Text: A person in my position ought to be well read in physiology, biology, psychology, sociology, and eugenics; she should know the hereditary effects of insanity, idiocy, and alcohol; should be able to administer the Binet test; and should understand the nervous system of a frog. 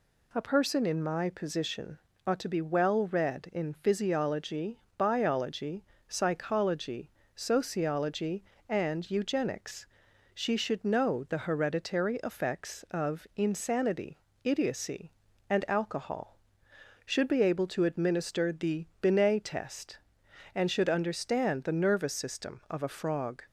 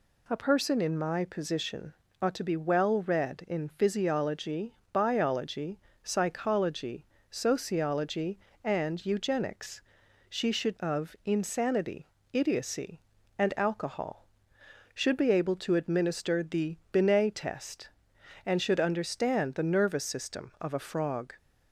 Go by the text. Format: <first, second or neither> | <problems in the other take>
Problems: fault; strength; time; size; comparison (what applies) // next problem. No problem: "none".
first | pauses between "position" and "ought"; slight; at 1.9 s; 0.28 s long; slight in the first // skips "know the hereditary effects"; at 10.7 s // pauses between "the" and "Binet"; slight; at 16.7 s; 0.16 s long; slight in the first